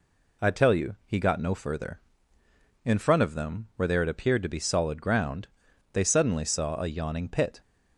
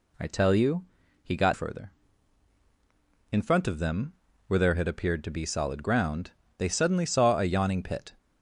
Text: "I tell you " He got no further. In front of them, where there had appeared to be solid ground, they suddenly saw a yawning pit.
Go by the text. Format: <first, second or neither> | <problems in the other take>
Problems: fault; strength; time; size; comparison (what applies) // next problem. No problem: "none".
first | skips "no"; at 1.5 s